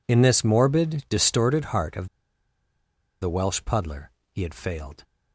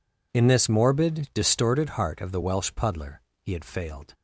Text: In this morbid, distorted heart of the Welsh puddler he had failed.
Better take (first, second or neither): second